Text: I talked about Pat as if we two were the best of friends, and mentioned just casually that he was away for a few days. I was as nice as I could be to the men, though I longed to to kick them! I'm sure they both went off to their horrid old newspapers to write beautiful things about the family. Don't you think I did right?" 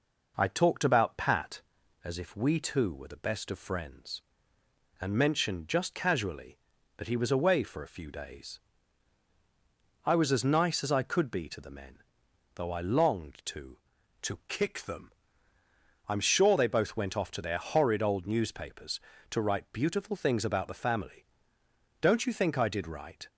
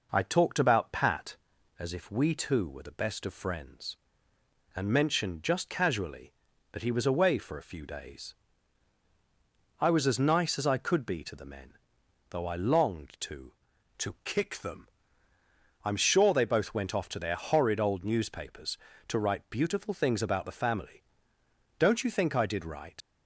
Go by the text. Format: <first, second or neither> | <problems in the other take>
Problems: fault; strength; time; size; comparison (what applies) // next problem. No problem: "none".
first | leaves "right" unfinished; at 23.0 s; 55 ms